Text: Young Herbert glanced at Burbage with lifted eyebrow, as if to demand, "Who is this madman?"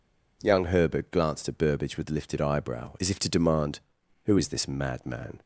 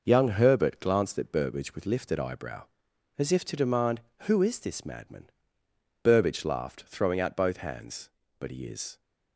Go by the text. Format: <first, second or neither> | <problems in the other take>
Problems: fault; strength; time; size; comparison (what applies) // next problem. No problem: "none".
first | goes on to say "Burbage laughed throwing out both hands But he is"; strong; from 6.0 s on; 2.9 s long